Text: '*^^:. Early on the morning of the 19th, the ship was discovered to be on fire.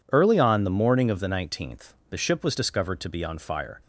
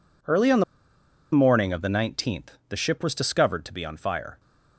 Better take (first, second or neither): first